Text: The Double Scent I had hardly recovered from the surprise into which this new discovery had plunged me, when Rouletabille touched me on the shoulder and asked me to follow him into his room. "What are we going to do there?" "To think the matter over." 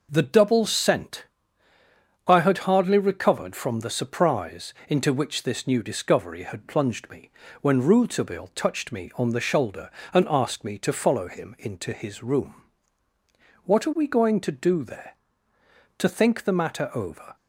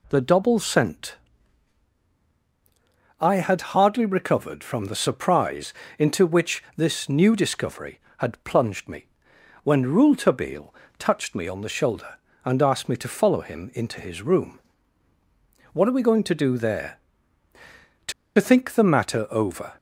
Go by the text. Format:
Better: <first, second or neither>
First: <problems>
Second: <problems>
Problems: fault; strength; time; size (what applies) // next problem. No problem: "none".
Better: first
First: pauses between "Scent" and "I"; at 1.2 s; 1.0 s long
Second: pauses between "Scent" and "I"; strong; at 1.1 s; 2.0 s long // pauses between "surprise" and "into"; slight; at 5.7 s; 0.24 s long // pauses between "Rouletabille" and "touched"; slight; at 10.7 s; 0.28 s long // pauses between "To" and "think"; slight; at 18.1 s; 0.26 s long